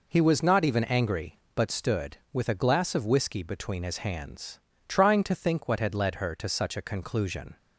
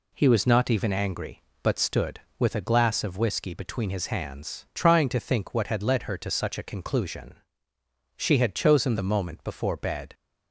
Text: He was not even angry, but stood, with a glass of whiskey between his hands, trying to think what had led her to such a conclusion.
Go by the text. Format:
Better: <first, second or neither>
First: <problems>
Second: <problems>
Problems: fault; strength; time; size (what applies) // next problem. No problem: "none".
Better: first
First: none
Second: goes on to say "She had chosen the moment before bed"; strong; from 8.1 s on; 1.9 s long